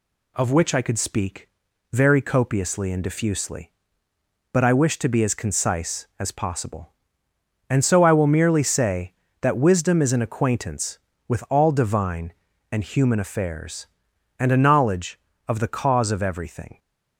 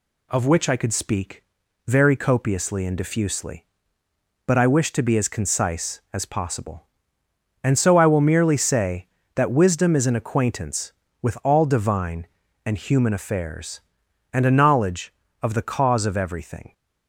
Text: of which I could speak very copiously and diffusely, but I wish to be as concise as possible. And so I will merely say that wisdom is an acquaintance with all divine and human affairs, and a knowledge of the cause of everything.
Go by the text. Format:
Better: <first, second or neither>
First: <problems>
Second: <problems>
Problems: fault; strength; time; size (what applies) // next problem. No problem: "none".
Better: neither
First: pauses between "speak" and "very"; at 1.4 s; 0.42 s long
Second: pauses between "speak" and "very"; at 1.4 s; 0.42 s long